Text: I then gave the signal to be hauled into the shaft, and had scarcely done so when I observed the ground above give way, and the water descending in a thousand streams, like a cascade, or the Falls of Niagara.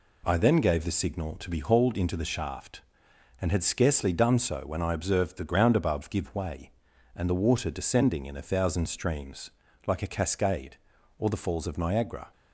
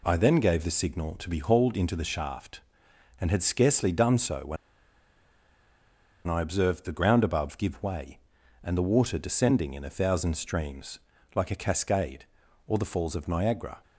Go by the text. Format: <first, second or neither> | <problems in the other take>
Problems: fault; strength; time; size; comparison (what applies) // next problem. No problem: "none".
first | pauses between "when" and "I"; strong; at 4.5 s; 1.7 s long